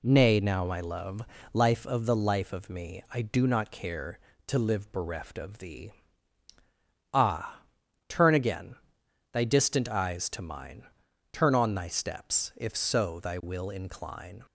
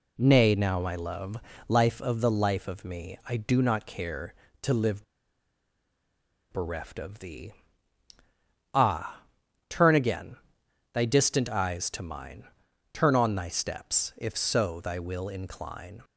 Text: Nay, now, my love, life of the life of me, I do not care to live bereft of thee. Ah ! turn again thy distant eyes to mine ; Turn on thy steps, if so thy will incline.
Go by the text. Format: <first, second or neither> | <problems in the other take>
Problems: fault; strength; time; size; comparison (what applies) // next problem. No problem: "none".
first | pauses between "live" and "bereft"; strong; at 5.0 s; 1.4 s long // pauses between "again" and "thy"; noticeable; at 10.3 s; 0.58 s long; noticeable in the first